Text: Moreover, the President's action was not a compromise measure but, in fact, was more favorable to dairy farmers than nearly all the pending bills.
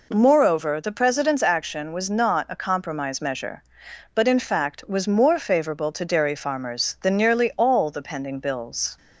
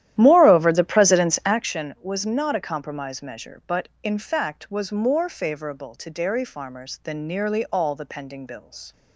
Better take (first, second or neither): first